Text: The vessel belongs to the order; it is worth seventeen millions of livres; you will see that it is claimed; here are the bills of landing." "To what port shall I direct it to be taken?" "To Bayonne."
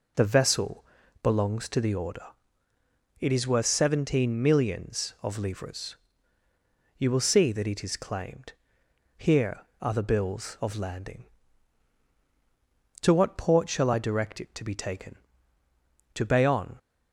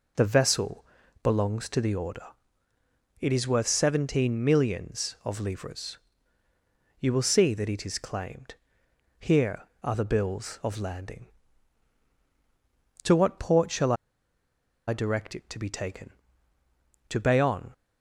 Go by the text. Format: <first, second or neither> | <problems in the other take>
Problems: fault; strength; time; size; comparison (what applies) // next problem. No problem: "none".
first | pauses between "vessel" and "belongs"; at 0.8 s; 0.38 s long; also in the first // pauses between "shall" and "I"; noticeable; at 13.9 s; 0.94 s long